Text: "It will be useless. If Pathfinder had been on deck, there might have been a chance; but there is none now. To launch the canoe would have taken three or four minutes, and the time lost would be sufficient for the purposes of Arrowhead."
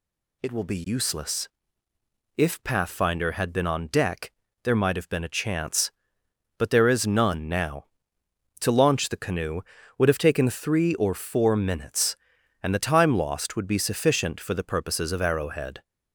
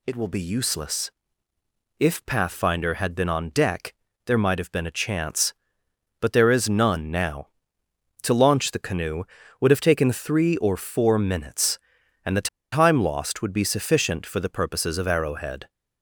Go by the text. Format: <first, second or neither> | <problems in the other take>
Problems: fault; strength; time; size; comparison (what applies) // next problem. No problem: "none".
first | pauses between "the" and "time"; slight; at 12.4 s; 0.23 s long